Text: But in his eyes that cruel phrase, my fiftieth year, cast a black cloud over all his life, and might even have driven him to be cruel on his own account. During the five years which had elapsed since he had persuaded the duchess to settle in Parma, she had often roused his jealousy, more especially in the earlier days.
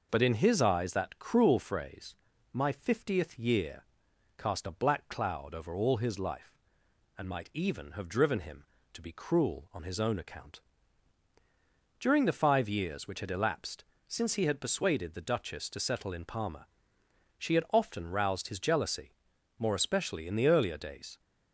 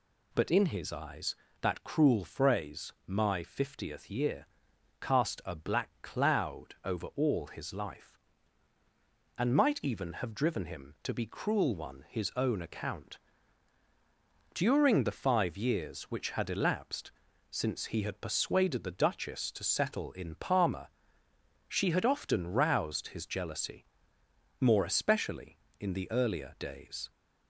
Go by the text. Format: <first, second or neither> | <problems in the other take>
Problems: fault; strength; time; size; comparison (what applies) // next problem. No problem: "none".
first | says "one" for "on"; at 11.7 s // pauses between "elapsed" and "since"; at 17.1 s; 0.38 s long; slight in the first